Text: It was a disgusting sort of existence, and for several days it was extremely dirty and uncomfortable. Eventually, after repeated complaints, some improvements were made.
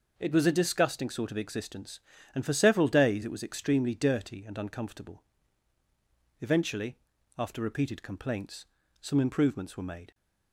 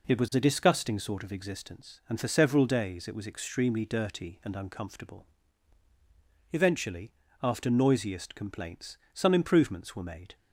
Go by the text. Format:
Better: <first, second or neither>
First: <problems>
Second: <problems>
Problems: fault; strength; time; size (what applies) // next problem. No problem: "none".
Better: first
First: none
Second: says "noisiest" for "repeated"; at 7.6 s